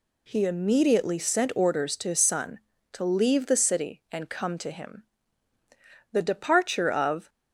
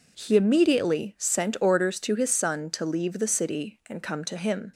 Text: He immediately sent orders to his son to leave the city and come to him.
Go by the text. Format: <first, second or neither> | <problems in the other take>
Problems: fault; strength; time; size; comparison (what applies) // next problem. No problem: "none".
second | goes on to say "The departure of"; noticeable; from 6.1 s on; 1.1 s long